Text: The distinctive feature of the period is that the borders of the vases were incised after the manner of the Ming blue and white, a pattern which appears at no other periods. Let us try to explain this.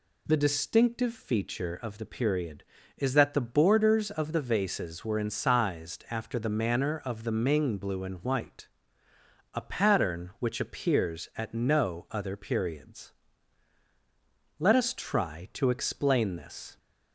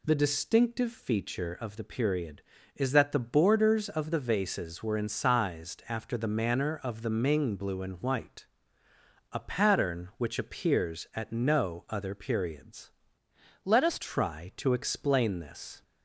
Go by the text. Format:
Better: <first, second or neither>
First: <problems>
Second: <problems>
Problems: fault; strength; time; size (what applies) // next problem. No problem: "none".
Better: first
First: none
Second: changes voice from "Let" to "us"; from 13.6 to 14.0 s; 0.4 s long